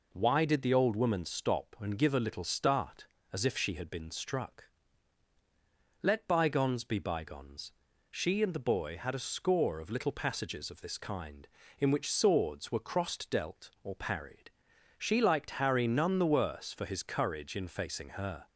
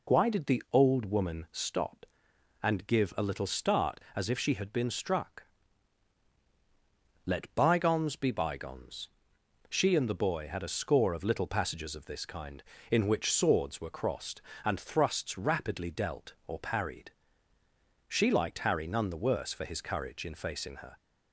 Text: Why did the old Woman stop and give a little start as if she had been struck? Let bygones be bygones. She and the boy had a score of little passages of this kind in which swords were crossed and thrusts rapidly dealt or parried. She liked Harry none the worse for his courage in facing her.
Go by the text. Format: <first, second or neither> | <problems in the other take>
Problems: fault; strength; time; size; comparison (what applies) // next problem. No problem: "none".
second | skips "and thrusts rapidly"; at 13.2 s